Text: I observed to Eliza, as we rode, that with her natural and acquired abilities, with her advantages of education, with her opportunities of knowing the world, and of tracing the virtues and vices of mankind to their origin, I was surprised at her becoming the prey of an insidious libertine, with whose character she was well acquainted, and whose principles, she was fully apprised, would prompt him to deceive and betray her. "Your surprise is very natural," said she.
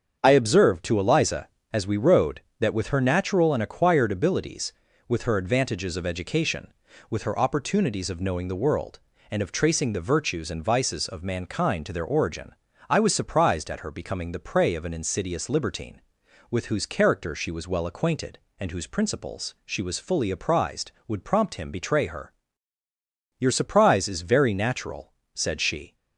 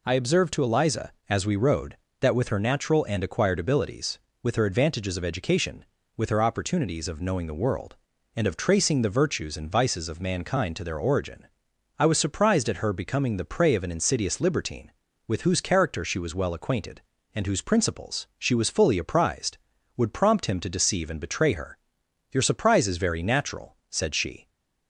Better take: second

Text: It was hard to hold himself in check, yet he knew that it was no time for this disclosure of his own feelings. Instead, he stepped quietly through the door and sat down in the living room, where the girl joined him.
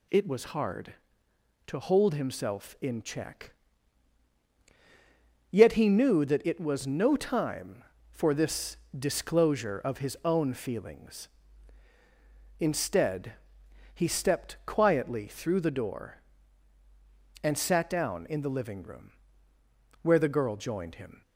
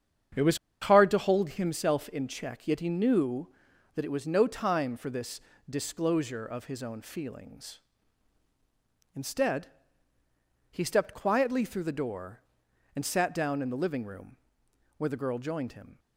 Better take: first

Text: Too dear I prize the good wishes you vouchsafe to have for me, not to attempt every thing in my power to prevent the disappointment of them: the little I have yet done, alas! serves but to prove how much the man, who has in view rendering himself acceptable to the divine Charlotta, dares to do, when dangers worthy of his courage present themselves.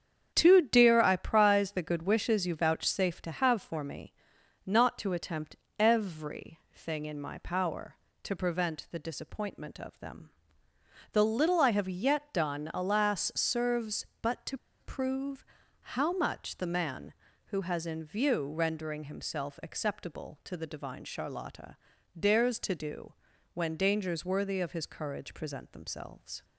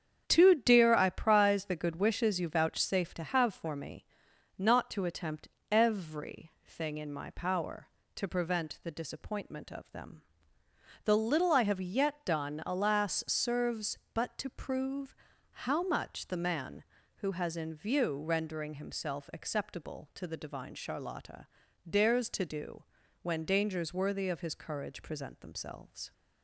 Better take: second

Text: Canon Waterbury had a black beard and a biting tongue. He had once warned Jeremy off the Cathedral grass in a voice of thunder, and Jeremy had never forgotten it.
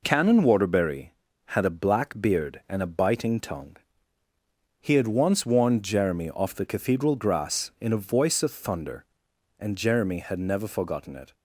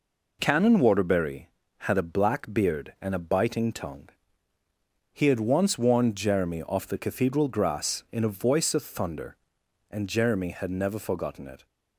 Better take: neither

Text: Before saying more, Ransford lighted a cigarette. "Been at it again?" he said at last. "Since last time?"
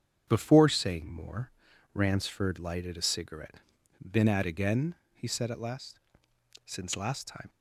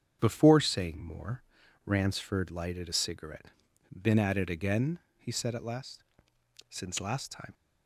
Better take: second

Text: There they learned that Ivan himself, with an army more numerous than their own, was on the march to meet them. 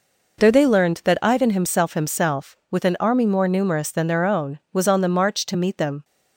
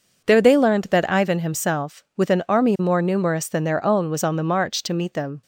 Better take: second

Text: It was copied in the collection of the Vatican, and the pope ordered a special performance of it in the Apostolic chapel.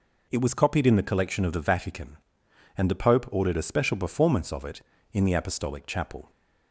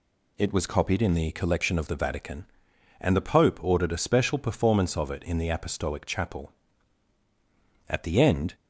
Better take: first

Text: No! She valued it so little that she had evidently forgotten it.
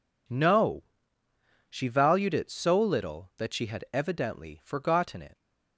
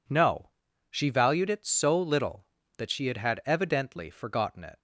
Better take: first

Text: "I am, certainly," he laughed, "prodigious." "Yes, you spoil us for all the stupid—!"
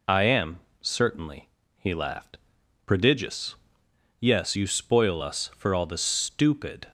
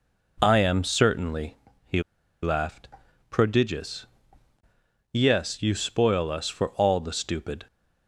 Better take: first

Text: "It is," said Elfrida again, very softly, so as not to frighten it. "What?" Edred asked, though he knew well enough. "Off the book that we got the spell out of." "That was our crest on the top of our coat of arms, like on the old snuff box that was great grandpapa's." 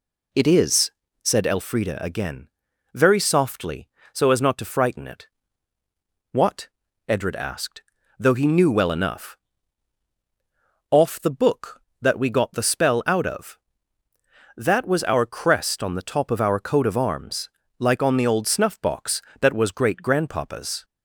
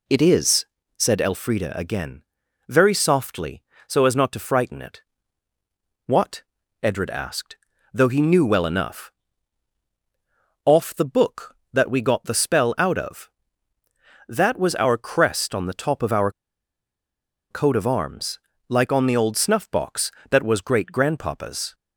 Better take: first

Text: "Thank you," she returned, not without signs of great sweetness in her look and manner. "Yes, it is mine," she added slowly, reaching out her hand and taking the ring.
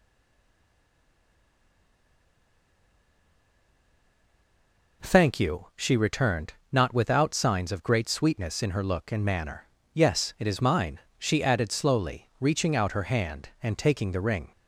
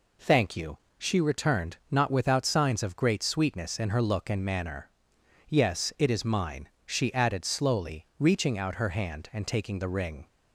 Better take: second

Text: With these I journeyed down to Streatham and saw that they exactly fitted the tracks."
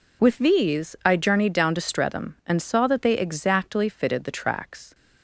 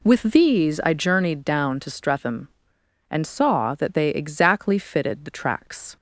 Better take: neither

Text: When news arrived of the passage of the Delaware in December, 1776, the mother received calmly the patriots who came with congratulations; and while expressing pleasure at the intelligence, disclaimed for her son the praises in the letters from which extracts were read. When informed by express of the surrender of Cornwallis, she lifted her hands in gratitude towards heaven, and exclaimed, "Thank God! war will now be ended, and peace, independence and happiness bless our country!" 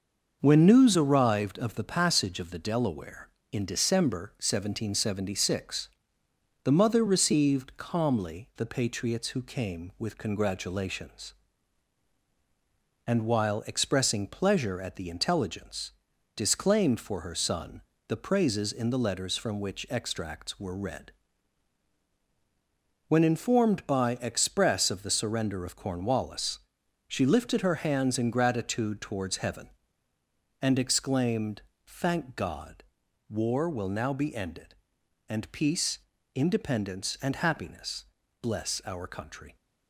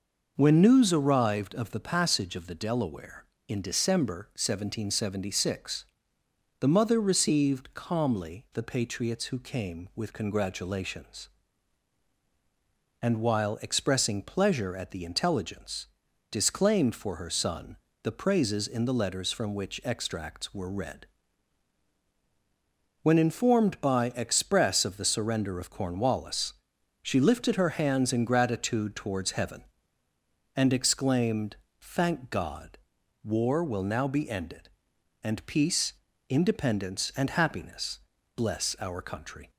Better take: second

